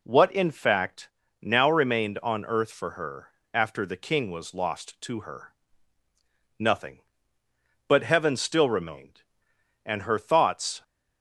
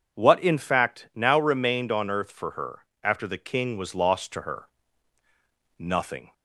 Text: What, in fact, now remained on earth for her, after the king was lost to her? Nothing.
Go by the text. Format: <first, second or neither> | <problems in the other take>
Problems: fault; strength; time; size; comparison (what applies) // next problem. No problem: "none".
second | goes on to say "But Heaven still remained and her thoughts"; strong; from 7.8 s on; 2.9 s long